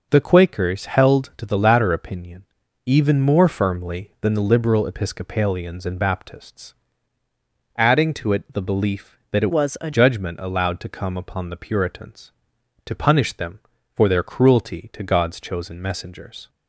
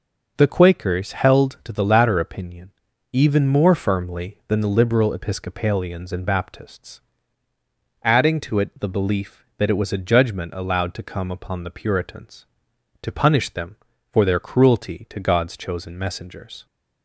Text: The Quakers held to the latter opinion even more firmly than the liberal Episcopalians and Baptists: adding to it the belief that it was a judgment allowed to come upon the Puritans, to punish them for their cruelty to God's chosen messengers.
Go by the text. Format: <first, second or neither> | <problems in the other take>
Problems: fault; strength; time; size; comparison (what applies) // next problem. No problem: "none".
second | pauses between "opinion" and "even"; at 2.4 s; 0.42 s long; also in the second // changes voice from "was" to "a"; from 9.5 to 9.9 s; 0.4 s long